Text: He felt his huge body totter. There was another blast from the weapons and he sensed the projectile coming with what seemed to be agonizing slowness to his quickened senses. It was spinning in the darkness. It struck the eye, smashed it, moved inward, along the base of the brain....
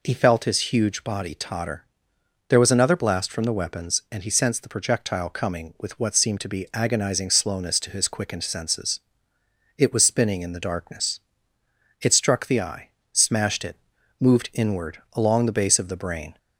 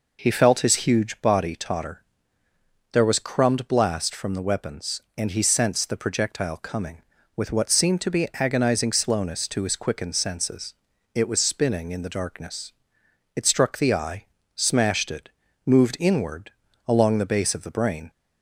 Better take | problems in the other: first | says "crumbed" for "another"; at 3.2 s

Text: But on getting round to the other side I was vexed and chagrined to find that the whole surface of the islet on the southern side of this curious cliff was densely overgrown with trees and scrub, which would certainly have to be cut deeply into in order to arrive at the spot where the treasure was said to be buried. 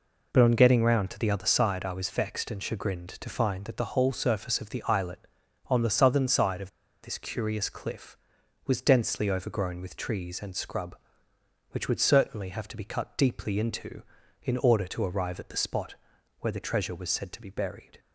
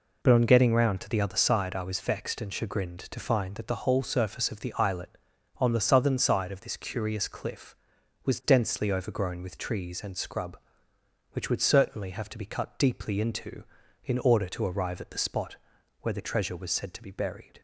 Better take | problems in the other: second | pauses between "of" and "this"; slight; at 6.6 s; 0.32 s long // pauses between "spot" and "where"; at 15.9 s; 0.44 s long; also in the second

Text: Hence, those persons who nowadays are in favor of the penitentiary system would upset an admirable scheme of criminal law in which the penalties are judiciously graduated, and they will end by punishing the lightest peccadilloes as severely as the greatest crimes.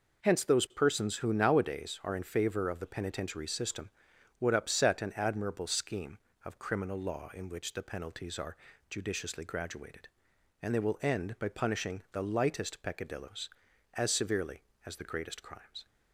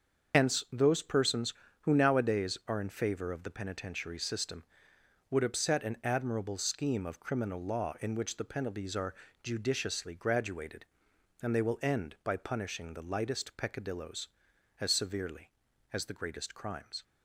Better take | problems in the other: first | loses the start of "Hence"; at 0.3 s; 75 ms // starts louder than the rest; until 1.4 s; 6.5 dB // pauses between "are" and "judiciously"; slight; at 9.1 s; 0.28 s long; slight in the first

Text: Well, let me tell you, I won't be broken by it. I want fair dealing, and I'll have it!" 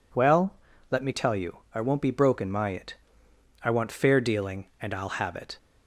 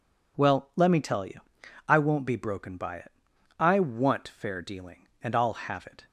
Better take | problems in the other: second | says "my" for "by"; at 2.5 s

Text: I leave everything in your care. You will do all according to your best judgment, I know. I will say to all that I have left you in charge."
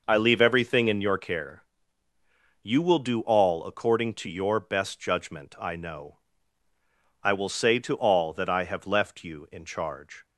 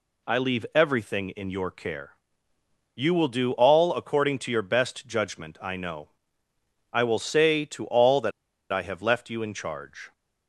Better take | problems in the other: first | pauses between "that" and "I"; at 8.3 s; 0.40 s long

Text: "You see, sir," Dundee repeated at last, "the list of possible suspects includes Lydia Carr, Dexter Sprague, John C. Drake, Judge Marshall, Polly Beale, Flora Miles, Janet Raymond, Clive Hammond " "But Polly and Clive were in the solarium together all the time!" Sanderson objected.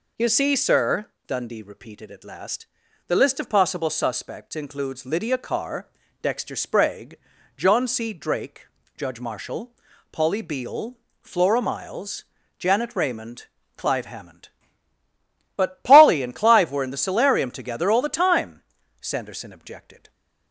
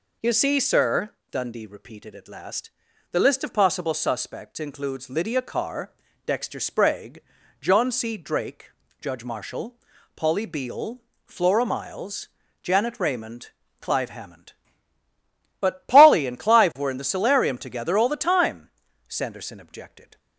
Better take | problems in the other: neither | none

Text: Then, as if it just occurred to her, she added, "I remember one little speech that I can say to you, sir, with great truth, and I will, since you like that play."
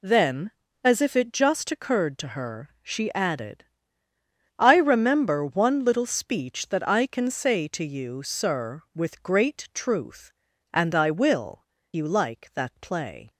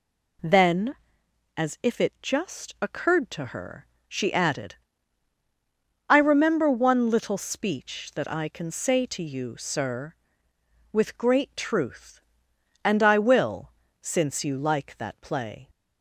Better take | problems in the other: second | skips "since"; at 11.7 s

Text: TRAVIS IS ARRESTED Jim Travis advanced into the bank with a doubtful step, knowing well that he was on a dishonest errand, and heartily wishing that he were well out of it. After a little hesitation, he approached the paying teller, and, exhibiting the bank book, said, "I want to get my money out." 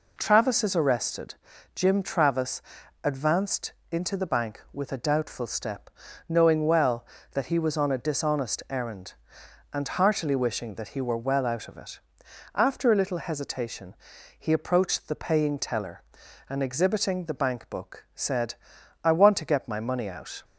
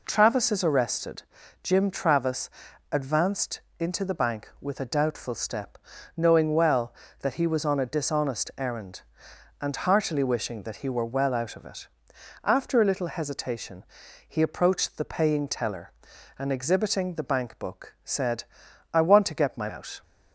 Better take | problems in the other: first | pauses between "ARRESTED" and "Jim"; at 1.2 s; 0.40 s long; also in the first // pauses between "Travis" and "advanced"; at 2.4 s; 0.44 s long; also in the first // pauses between "advanced" and "into"; slight; at 3.6 s; 0.18 s long; slight in the first // skips "money"; at 19.6 s

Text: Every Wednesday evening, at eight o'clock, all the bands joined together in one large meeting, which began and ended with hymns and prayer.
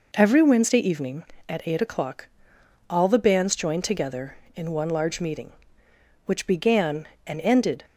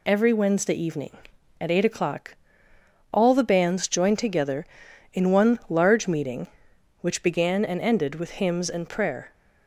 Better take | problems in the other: second | stops before "with hymns and prayer"; at 7.8 s

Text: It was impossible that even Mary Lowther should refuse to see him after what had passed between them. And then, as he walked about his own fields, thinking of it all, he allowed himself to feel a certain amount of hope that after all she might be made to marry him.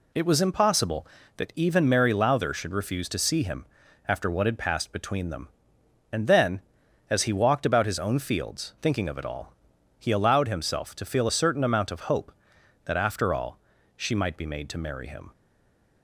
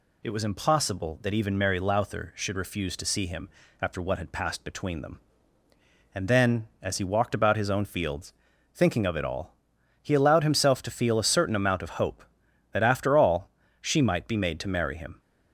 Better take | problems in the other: second | pauses between "him" and "after"; at 3.6 s; 0.42 s long; slight in the second // pauses between "all" and "she"; at 13.5 s; 0.38 s long; slight in the second // stays silent after the last word; slight; from 15.3 s on; 0.7 s long

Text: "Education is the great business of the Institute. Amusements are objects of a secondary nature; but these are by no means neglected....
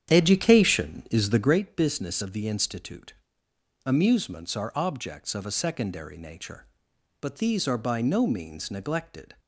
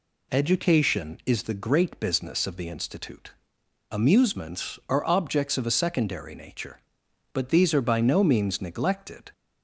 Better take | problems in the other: second | starts louder than the rest; strong; until 1.6 s; 9 dB

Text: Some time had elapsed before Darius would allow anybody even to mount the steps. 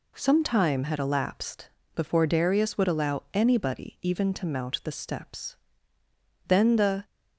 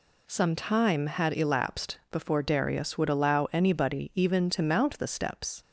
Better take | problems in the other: second | pauses between "elapsed" and "before"; slight; at 1.6 s; 0.28 s long // goes on to say "Then the"; from 6.4 s on; 0.58 s long

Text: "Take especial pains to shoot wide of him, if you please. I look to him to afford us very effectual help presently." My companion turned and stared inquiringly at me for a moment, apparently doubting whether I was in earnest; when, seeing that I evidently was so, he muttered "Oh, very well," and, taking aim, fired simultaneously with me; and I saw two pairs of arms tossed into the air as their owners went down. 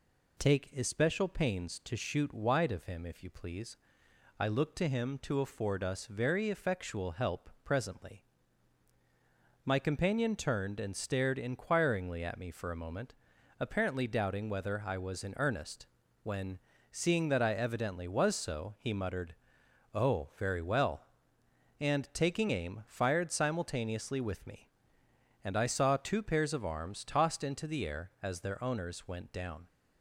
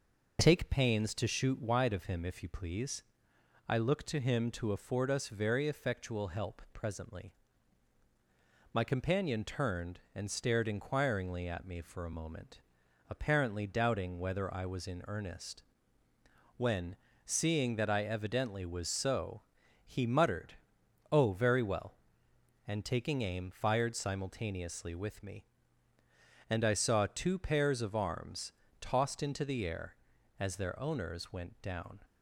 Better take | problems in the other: first | skips "especial"; at 0.7 s // pauses between "muttered" and "Oh"; noticeable; at 20.5 s; 0.58 s long; noticeable in the first // pauses between "arms" and "tossed"; slight; at 28.5 s; 0.26 s long

